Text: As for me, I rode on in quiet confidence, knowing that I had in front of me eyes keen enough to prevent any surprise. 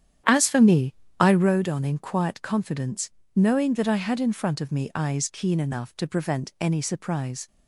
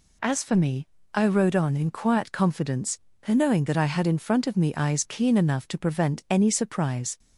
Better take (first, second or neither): second